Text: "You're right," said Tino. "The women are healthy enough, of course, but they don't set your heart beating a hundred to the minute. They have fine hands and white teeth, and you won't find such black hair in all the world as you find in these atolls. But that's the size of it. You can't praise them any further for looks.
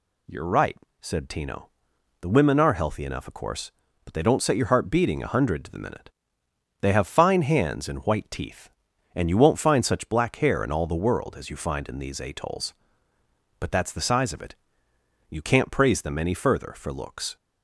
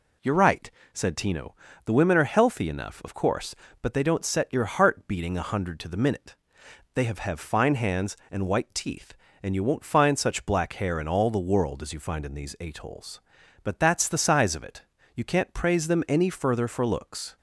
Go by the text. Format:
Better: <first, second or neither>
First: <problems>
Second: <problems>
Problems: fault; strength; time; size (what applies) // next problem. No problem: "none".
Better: first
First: none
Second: says "have" twice; at 7.1 s